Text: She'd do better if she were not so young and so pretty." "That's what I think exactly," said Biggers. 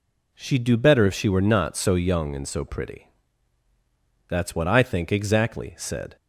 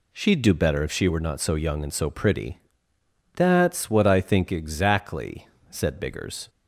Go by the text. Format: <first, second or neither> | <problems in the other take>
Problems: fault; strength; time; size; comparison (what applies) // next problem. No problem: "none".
second | stops before "Biggers"; at 6.1 s